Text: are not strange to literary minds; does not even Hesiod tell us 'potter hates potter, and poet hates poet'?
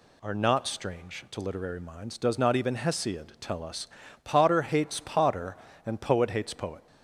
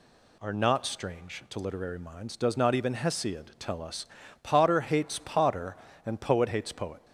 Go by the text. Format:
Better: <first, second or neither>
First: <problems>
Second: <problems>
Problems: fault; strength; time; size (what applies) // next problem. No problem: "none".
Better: neither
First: pauses between "us" and "potter"; slight; at 3.8 s; 0.36 s long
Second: pauses between "us" and "potter"; slight; at 4.0 s; 0.36 s long